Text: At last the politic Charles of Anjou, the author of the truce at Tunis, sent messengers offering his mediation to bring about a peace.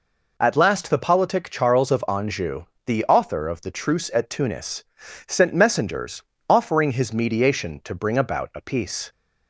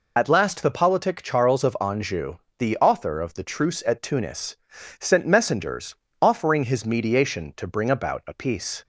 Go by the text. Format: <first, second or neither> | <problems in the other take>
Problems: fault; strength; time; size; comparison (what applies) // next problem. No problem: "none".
first | loses the start of "At"; at 0.1 s; 50 ms // pauses between "messengers" and "offering"; slight; at 5.9 s; 0.26 s long; slight in the first